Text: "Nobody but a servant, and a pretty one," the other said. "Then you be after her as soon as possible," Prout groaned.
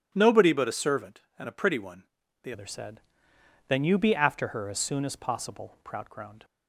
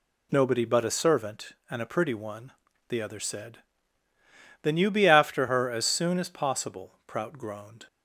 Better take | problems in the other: second | starts louder than the rest; strong; until 1.1 s; 10.5 dB // changes voice at "other"; from 2.5 s on; 3.9 s long

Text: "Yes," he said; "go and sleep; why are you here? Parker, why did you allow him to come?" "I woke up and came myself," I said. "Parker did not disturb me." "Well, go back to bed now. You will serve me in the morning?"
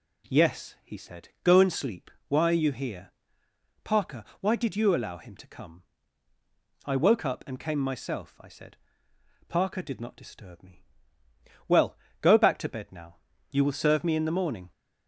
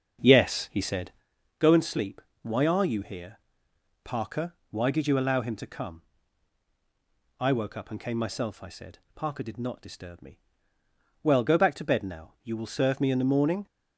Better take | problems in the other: first | starts louder than the rest; until 1.2 s; 6.5 dB

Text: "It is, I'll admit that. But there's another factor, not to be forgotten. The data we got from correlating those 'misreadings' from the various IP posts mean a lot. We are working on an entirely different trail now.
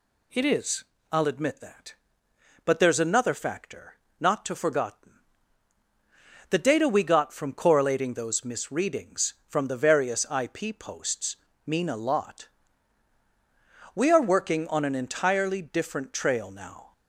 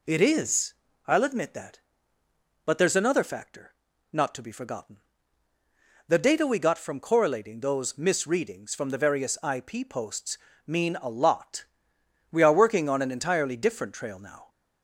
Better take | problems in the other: second | skips "be"; at 4.5 s // pauses between "posts" and "mean"; slight; at 11.3 s; 0.32 s long; slight in the second

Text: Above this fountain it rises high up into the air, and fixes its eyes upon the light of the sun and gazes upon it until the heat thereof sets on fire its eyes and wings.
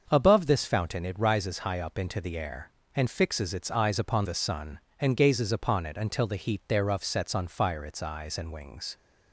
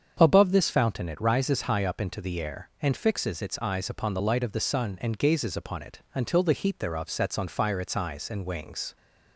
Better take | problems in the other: second | starts louder than the rest; until 1.0 s; 6.5 dB; strong in the second // skips "the light of"; at 4.2 s

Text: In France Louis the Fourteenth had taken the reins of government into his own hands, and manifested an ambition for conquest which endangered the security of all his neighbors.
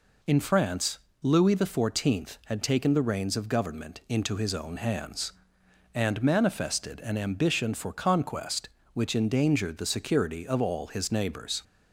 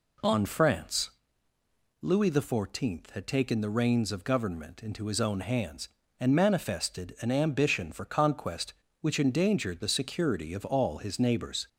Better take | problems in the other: first | says "On" for "In"; at 0.2 s // pauses between "France" and "Louis"; noticeable; at 1.1 s; 0.90 s long; slight in the first

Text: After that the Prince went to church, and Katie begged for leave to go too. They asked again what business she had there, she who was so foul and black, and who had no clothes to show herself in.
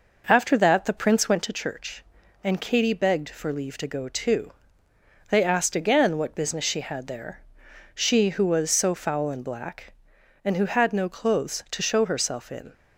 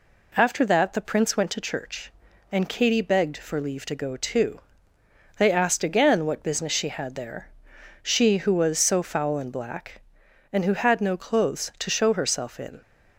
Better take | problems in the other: second | starts louder than the rest; noticeable; until 1.6 s; 5.5 dB

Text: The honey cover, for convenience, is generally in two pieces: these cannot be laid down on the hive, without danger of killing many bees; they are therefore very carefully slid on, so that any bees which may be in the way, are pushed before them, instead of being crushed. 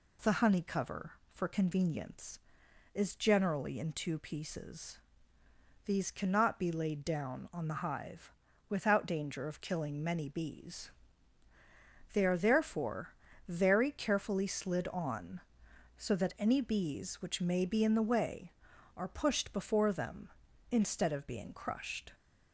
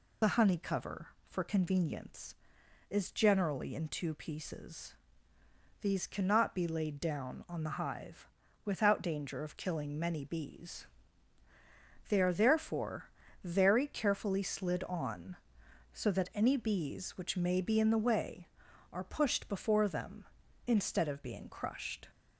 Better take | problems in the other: first | loses the start of "The"; at 0.2 s; 75 ms // pauses between "therefore" and "very"; slight; at 13.0 s; 0.34 s long; slight in the first

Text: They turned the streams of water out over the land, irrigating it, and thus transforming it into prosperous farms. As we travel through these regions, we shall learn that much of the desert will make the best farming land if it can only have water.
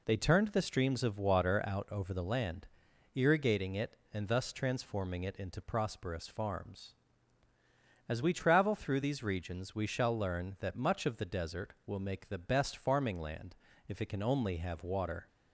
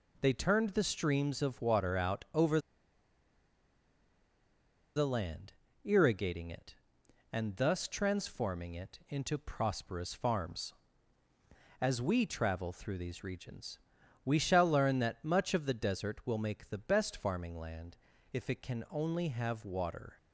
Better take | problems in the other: first | pauses between "over" and "the"; strong; at 2.5 s; 2.3 s long // pauses between "land" and "if"; at 17.9 s; 0.38 s long; slight in the first

